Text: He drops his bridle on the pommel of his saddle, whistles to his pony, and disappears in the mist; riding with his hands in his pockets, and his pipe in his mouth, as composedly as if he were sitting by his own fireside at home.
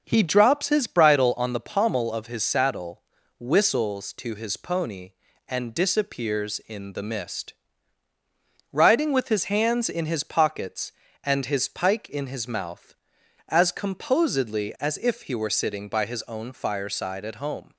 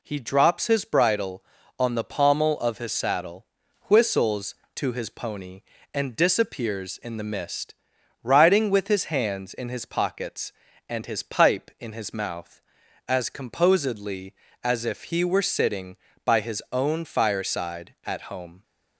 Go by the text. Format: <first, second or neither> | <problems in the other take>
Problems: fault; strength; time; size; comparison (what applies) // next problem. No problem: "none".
second | says "pike" for "pipe"; at 11.6 s